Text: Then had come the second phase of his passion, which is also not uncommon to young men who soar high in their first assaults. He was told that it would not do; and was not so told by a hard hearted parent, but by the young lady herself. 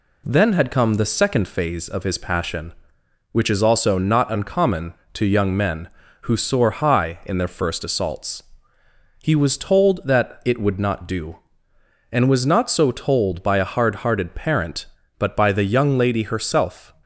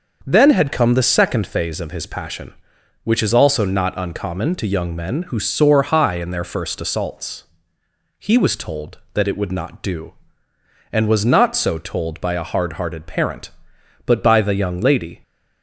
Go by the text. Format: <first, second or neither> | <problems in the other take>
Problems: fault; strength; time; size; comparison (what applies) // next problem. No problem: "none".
first | starts louder than the rest; until 1.2 s; 6.5 dB // stops before "herself"; at 15.2 s